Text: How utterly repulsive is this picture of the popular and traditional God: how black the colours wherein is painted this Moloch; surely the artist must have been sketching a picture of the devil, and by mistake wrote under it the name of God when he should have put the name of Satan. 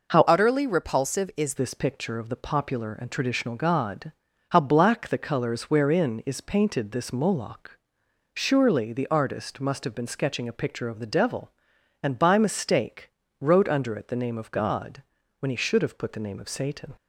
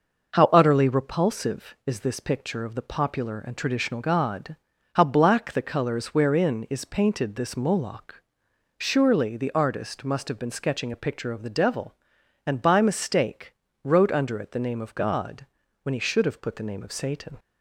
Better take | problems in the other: second | changes voice from "utterly" to "is"; from 0.2 to 1.5 s; 1.3 s long // pauses between "mistake" and "wrote"; slight; at 13.1 s; 0.28 s long; slight in the second // pauses between "God" and "when"; slight; at 15.0 s; 0.34 s long; slight in the second

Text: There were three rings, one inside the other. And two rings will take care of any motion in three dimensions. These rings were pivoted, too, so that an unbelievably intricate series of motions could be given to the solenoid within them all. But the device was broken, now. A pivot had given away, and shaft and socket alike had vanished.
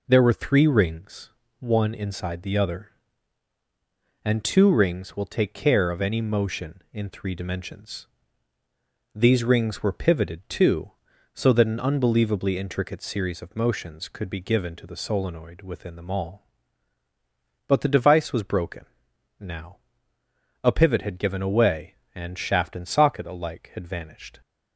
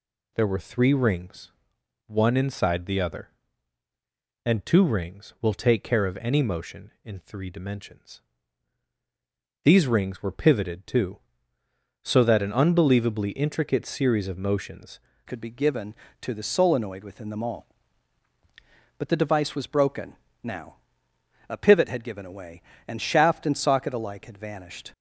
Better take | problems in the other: first | changes voice at "could"; from 15.2 s on; 9.7 s long

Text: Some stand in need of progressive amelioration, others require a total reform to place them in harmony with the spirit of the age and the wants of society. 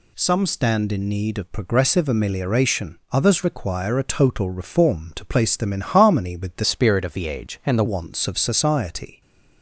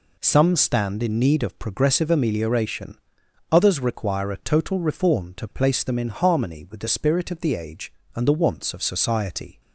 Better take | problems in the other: second | changes voice from "spirit" to "the"; from 6.6 to 7.8 s; 1.2 s long

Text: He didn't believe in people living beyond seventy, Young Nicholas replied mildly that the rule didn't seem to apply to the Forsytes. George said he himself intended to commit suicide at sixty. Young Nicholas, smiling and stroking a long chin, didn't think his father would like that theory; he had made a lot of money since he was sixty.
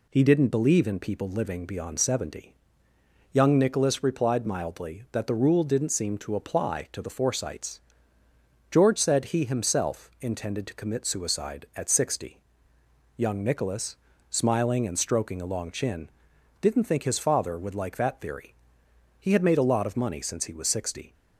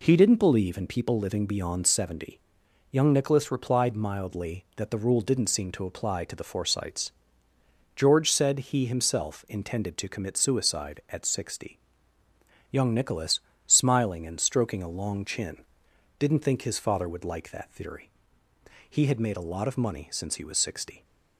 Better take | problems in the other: neither | none

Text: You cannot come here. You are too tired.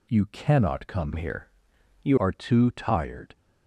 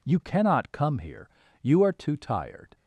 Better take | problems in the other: second | changes voice from "here" to "You"; from 1.1 to 2.1 s; 1.0 s long

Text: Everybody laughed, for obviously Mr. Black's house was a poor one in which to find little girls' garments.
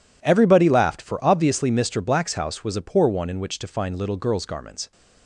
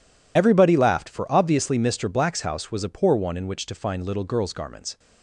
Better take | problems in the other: first | loses the start of "Everybody"; at 0.3 s; 55 ms

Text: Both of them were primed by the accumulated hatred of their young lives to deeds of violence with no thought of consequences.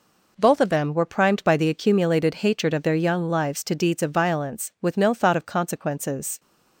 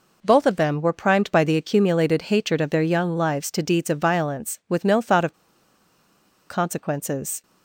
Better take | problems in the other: first | pauses between "of" and "consequences"; at 5.3 s; 1.1 s long

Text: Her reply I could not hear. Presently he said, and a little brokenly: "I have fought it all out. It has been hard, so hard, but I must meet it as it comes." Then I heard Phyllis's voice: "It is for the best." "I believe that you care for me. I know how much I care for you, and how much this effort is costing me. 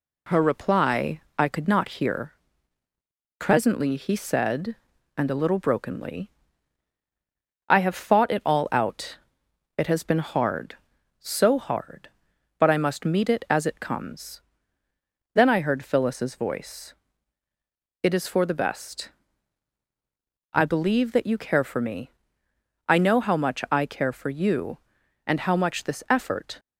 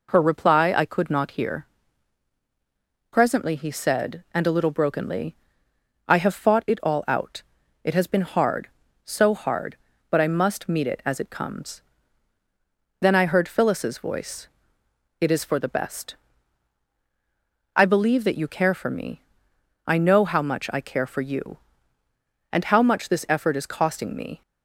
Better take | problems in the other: second | pauses between "reply" and "I"; slight; at 1.2 s; 0.16 s long // stops before "is costing me"; at 26.5 s

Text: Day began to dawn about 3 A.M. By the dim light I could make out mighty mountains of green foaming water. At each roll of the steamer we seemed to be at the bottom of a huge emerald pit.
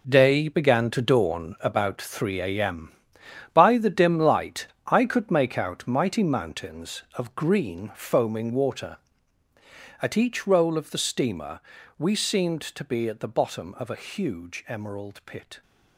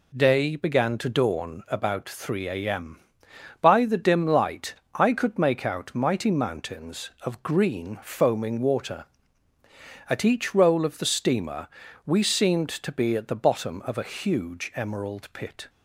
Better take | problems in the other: second | gets quieter; strong; throughout; 10.5 dB // pauses between "light" and "I"; slight; at 4.6 s; 0.18 s long; slight in the second // pauses between "steamer" and "we"; at 11.5 s; 0.38 s long; also in the second

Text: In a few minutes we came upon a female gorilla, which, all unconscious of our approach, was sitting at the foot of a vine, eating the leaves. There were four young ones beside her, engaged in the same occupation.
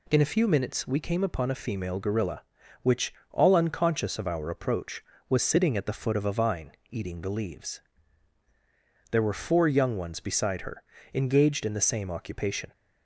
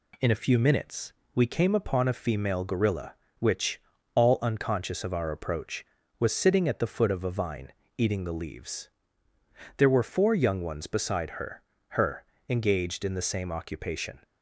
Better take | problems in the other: first | pauses between "minutes" and "we"; slight; at 1.1 s; 0.22 s long // says "her" twice; at 11.8 s

